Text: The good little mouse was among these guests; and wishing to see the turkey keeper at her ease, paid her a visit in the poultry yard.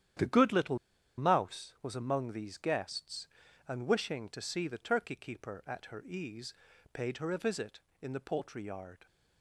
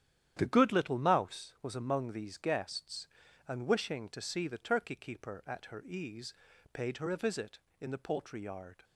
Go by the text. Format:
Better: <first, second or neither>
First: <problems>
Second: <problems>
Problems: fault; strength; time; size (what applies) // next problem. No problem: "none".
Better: second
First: starts louder than the rest; strong; until 1.6 s; 10 dB // pauses between "little" and "mouse"; at 0.7 s; 0.41 s long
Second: starts louder than the rest; strong; until 1.3 s; 10 dB